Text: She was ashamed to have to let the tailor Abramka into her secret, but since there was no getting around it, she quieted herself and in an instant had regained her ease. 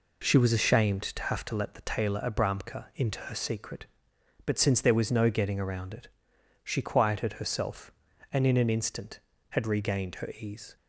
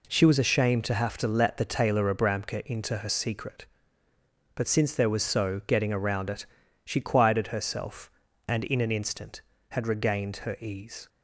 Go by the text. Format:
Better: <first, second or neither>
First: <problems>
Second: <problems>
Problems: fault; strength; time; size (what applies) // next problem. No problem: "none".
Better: first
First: none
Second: says "so" for "no"; at 5.2 s